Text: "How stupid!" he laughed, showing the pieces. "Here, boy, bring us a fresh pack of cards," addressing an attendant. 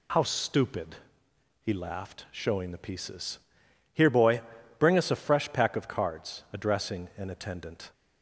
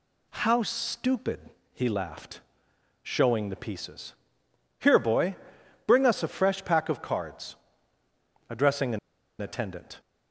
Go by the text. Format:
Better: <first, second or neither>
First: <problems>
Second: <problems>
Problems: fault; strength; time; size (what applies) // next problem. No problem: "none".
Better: first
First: none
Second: pauses between "an" and "attendant"; at 8.9 s; 0.43 s long